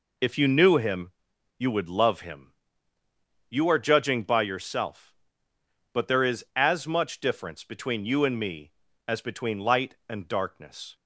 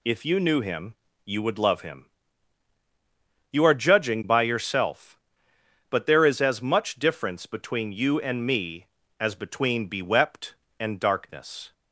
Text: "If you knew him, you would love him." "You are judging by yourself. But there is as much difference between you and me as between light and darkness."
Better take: first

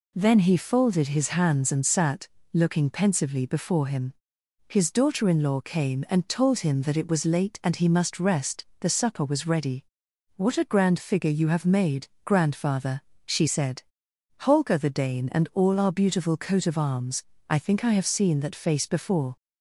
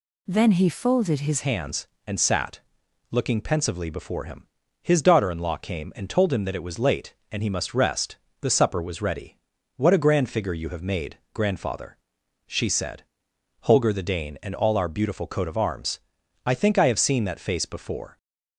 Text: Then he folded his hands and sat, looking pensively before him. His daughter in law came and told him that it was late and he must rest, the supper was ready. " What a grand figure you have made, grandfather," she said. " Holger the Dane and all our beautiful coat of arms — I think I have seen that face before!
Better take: first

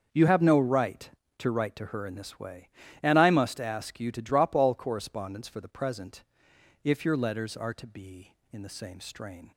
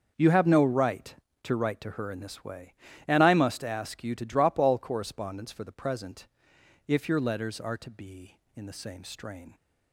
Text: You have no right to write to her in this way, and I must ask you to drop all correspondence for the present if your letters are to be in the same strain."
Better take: neither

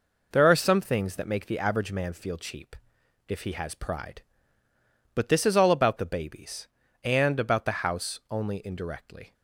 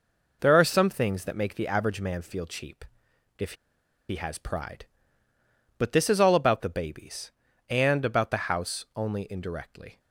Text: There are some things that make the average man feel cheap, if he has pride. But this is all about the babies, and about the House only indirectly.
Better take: first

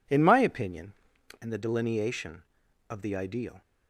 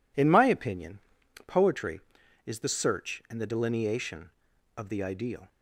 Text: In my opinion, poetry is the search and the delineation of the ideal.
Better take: second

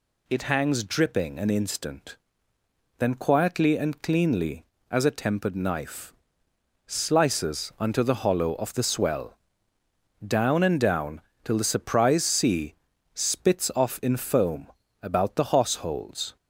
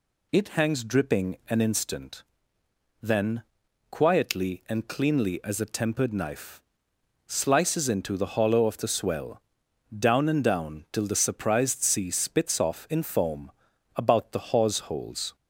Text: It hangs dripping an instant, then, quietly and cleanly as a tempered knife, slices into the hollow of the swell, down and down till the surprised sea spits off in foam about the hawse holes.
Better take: second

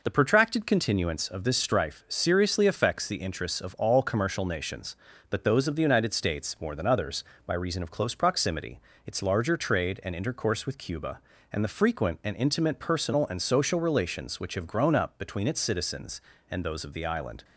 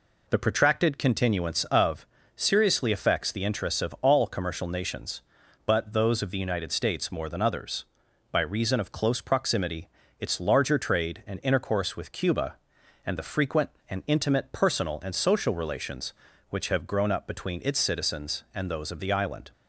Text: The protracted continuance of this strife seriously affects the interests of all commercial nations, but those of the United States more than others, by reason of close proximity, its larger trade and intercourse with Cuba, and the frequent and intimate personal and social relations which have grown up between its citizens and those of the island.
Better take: first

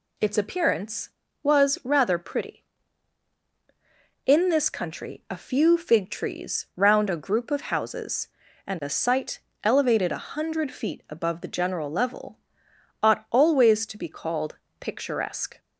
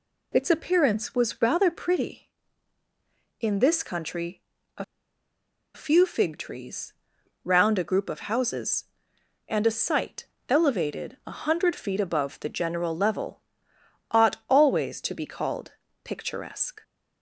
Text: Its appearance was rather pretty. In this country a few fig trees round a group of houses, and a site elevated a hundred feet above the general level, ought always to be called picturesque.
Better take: first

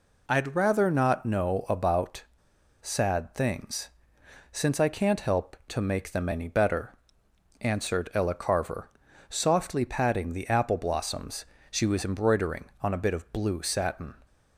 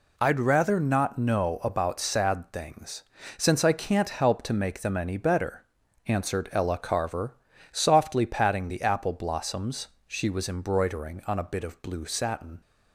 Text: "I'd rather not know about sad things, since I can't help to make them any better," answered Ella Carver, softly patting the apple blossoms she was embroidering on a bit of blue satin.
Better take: second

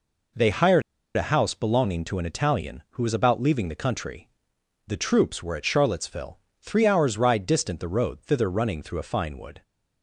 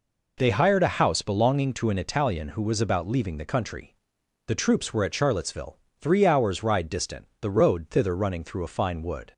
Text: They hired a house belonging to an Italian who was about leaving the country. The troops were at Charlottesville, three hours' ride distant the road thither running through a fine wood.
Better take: second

